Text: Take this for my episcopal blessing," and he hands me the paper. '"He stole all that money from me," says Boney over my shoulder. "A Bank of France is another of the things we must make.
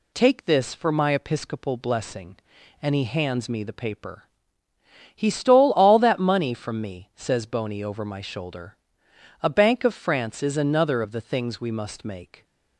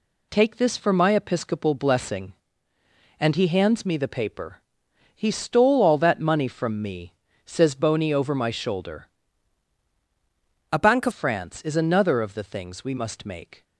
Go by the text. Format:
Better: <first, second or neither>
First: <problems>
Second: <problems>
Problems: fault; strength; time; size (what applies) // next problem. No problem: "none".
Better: first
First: none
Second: changes voice from "A" to "of"; from 10.7 to 11.1 s; 0.4 s long